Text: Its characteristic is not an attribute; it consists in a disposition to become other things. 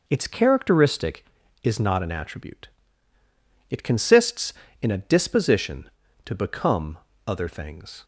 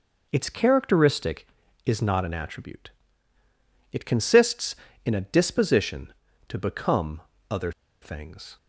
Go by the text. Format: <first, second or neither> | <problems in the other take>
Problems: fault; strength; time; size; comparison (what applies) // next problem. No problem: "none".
first | pauses between "become" and "other"; slight; at 7.2 s; 0.26 s long; slight in the first // pauses between "other" and "things"; slight; at 7.7 s; 0.31 s long